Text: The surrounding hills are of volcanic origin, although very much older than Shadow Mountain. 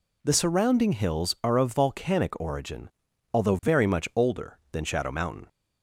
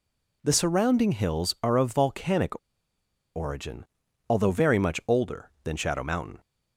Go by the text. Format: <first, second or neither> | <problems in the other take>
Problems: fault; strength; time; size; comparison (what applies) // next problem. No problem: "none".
first | pauses between "volcanic" and "origin"; noticeable; at 2.5 s; 0.77 s long